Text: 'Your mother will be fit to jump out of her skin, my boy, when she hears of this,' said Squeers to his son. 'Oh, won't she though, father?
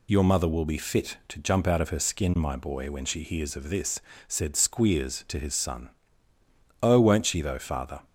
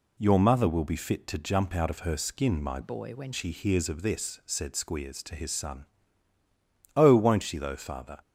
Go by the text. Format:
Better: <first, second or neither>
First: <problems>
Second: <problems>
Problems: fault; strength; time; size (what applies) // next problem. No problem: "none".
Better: first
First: none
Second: changes voice from "boy" to "when"; from 2.8 to 3.3 s; 0.5 s long